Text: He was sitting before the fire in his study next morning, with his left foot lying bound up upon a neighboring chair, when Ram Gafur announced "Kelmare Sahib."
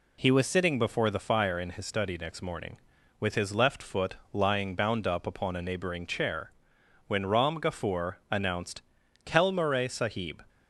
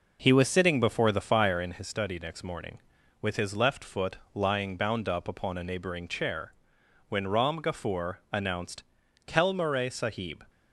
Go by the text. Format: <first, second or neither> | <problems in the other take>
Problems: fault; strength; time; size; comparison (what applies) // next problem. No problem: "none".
first | starts louder than the rest; noticeable; until 1.8 s; 5.5 dB // pauses between "foot" and "lying"; slight; at 4.1 s; 0.18 s long; slight in the first // pauses between "announced" and "Kelmare"; at 8.8 s; 0.44 s long; also in the first